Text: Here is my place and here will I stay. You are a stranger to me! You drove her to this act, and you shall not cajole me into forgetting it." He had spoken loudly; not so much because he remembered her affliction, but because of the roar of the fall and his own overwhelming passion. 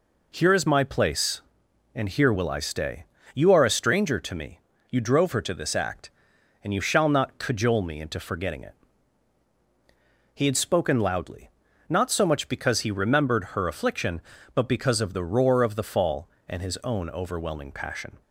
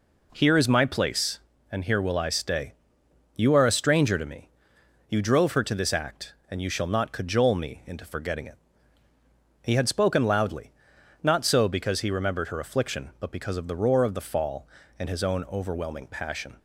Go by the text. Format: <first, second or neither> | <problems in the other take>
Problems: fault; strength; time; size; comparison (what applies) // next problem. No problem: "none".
first | skips "much"; at 11.6 s